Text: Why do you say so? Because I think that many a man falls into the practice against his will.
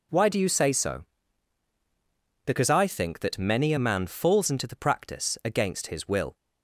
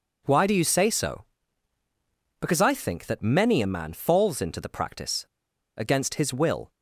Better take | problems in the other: first | pauses between "practice" and "against"; noticeable; at 5.2 s; 0.51 s long

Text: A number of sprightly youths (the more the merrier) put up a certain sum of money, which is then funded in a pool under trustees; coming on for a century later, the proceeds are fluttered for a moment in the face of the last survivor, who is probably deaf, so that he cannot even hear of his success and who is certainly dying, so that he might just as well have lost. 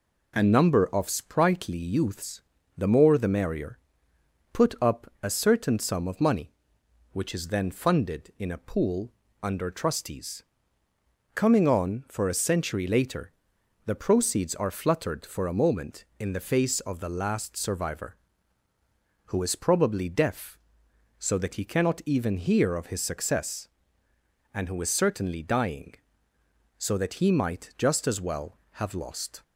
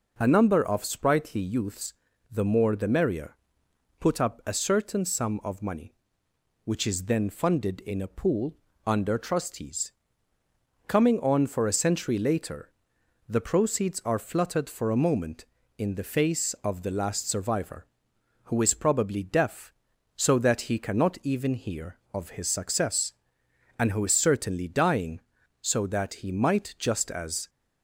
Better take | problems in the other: first | pauses between "pool" and "under"; slight; at 8.5 s; 0.30 s long; slight in the first // stops before "well have lost"; at 27.4 s

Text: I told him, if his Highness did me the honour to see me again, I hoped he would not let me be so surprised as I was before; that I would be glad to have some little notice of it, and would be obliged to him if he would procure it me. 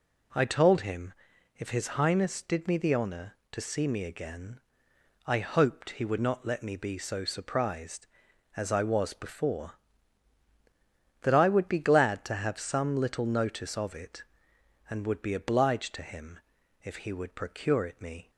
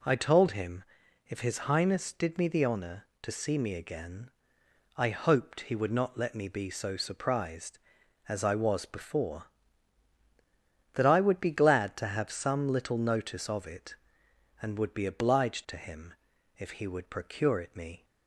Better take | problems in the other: neither | pauses between "him" and "if"; noticeable; the same in both

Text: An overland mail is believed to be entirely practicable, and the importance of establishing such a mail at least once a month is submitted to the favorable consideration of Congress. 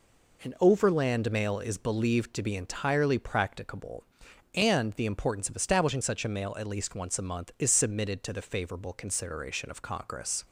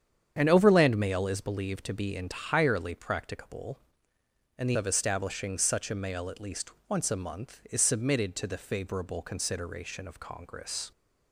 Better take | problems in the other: first | starts louder than the rest; strong; until 1.3 s; 8.5 dB // skips "importance"; at 4.7 s // pauses between "least" and "once"; slight; at 6.7 s; 0.18 s long

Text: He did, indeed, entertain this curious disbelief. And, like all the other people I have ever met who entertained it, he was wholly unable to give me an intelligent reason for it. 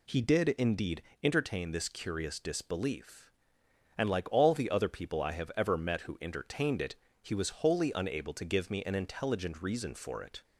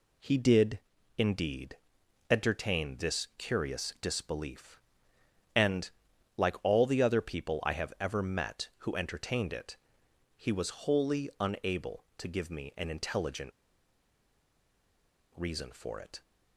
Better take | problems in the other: first | pauses between "intelligent" and "reason"; strong; at 13.5 s; 1.8 s long

